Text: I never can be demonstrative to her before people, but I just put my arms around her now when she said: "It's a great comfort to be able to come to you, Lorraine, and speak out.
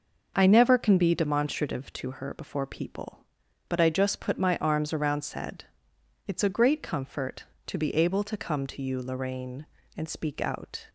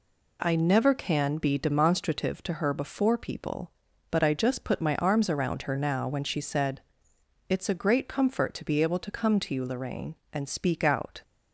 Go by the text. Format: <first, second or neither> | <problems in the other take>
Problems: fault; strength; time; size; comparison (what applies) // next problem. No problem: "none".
second | starts louder than the rest; noticeable; until 1.3 s; 6 dB // skips "her now when she"; at 5.2 s